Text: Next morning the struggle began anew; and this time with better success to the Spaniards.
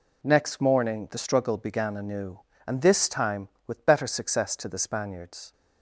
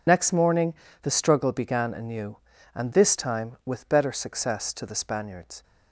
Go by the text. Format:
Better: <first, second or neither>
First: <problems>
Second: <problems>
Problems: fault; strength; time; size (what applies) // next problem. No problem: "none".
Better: first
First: none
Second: loses the start of "Next"; at 0.0 s; 55 ms // pauses between "morning" and "the"; slight; at 0.7 s; 0.28 s long